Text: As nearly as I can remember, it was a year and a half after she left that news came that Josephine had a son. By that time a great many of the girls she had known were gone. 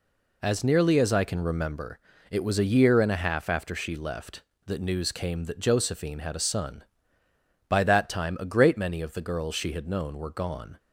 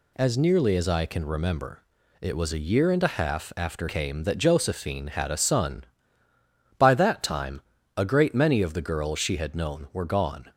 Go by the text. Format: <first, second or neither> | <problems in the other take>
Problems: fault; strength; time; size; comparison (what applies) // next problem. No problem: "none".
first | skips "she left that news"; at 3.8 s // pauses between "time" and "a"; slight; at 7.6 s; 0.36 s long